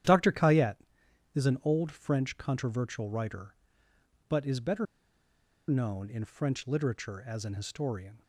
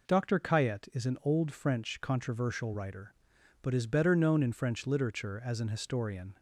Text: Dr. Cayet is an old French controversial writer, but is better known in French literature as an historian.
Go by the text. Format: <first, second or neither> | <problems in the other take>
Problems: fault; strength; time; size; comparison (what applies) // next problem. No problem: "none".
second | starts louder than the rest; strong; until 1.6 s; 11.5 dB // pauses between "better" and "known"; noticeable; at 4.8 s; 0.82 s long